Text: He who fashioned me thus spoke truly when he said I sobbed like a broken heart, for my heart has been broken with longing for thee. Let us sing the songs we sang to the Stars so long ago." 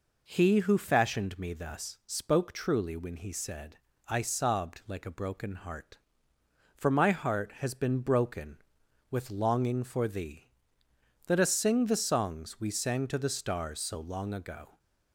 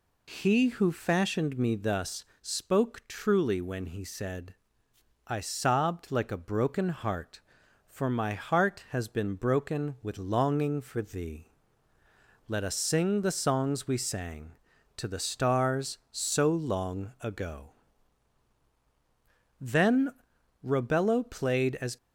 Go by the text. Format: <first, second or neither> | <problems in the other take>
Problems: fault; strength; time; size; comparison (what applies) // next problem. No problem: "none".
first | pauses between "thus" and "spoke"; slight; at 2.2 s; 0.20 s long // pauses between "said" and "I"; noticeable; at 4.5 s; 0.72 s long; slight in the first // goes on to say "Then Robello played as"; strong; from 19.6 s on; 2.3 s long